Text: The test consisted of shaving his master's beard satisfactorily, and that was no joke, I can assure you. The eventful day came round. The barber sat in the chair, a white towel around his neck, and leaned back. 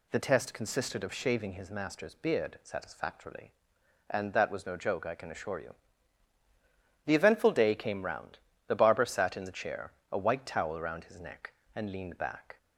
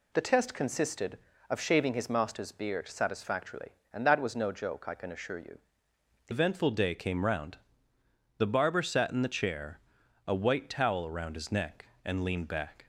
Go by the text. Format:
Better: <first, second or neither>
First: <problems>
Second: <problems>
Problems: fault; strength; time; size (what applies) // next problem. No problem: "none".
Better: first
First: none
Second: changes voice at "eventful"; from 6.3 s on; 6.5 s long